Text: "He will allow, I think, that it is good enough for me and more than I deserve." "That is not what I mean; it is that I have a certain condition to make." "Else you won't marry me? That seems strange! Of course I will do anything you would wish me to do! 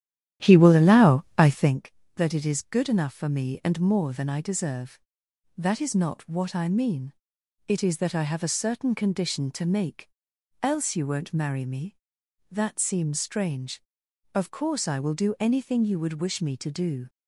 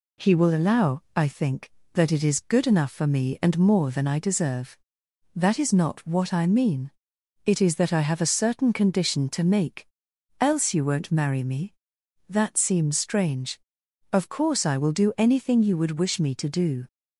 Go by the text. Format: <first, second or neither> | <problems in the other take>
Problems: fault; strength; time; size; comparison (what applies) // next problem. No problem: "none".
second | starts louder than the rest; strong; until 1.8 s; 11.5 dB